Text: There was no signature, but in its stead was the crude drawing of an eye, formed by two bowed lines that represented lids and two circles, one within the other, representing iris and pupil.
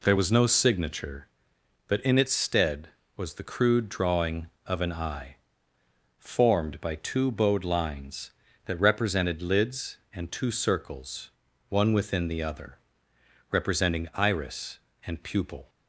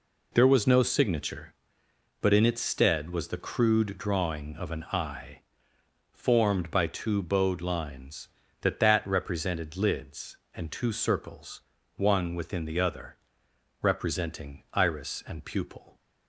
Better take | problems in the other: first | says "that" twice; at 8.7 s

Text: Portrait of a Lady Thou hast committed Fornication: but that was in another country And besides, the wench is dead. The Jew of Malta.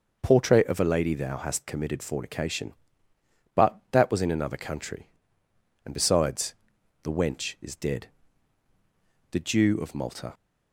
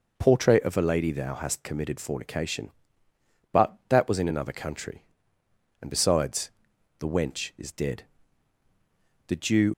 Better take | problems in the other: first | stops before "of Malta"; at 9.7 s

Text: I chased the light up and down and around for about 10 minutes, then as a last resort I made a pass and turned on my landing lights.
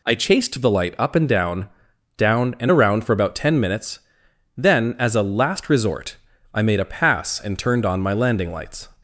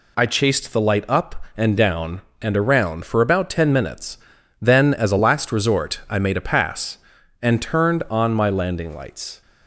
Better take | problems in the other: second | says "down" twice; at 2.1 s // pauses between "resort" and "I"; slight; at 6.1 s; 0.36 s long

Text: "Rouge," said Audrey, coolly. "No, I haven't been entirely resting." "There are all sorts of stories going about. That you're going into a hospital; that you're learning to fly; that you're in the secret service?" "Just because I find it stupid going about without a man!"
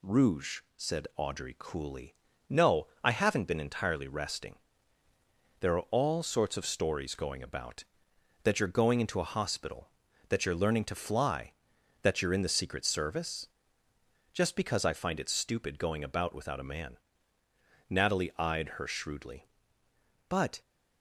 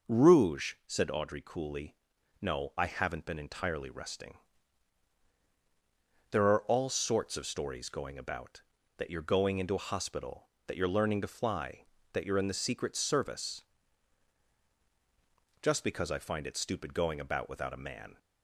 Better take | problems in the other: second | goes on to say "Natalie eyed her shrewdly but"; strong; from 17.8 s on; 2.7 s long

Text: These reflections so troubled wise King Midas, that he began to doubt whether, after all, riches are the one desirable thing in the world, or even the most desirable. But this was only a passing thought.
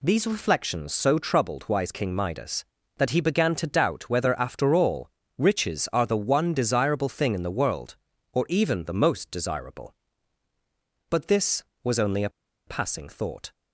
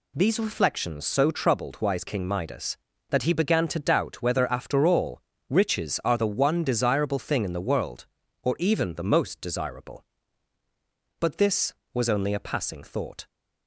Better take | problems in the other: second | pauses between "a" and "passing"; at 12.3 s; 0.36 s long

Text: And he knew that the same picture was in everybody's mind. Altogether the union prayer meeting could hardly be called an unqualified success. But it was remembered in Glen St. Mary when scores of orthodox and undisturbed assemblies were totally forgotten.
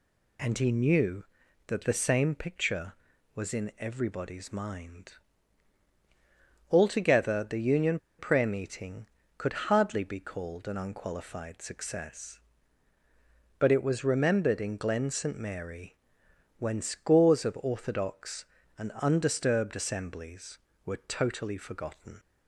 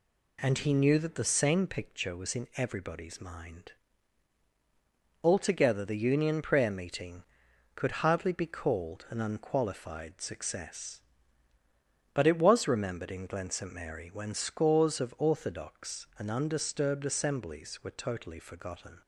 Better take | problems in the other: second | pauses between "union" and "prayer"; slight; at 7.9 s; 0.20 s long // pauses between "Mary" and "when"; noticeable; at 15.9 s; 0.62 s long

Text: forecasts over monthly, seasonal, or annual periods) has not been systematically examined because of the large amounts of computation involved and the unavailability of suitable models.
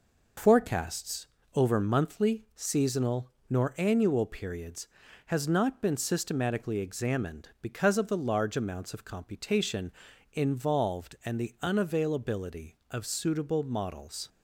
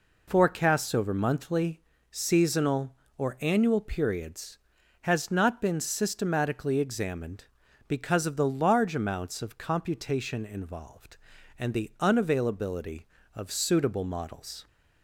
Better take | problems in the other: second | pauses between "forecasts" and "over"; slight; at 1.2 s; 0.30 s long // says "nor" for "or"; at 3.5 s // pauses between "computation" and "involved"; at 9.9 s; 0.42 s long

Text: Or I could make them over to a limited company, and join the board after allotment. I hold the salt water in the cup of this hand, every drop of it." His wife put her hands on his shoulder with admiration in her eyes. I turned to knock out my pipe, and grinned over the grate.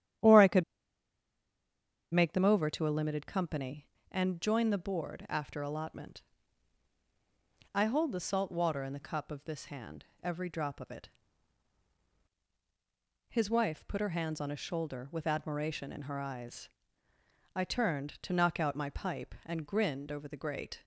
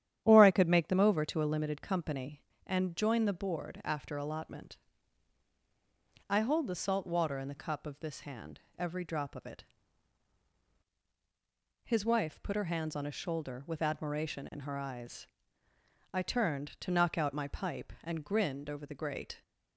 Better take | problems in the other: second | starts louder than the rest; strong; until 2.7 s; 10.5 dB; strong in the second // pauses between "could" and "make"; strong; at 0.6 s; 1.5 s long

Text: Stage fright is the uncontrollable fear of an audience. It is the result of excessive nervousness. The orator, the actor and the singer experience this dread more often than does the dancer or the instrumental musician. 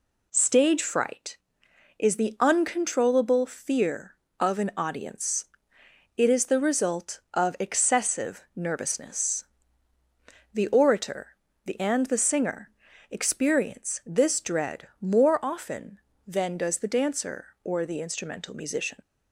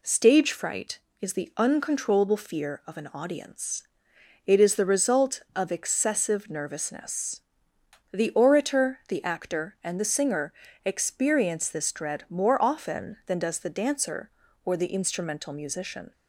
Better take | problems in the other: second | skips "actor"; at 11.8 s // pauses between "singer" and "experience"; at 12.6 s; 0.42 s long; slight in the second

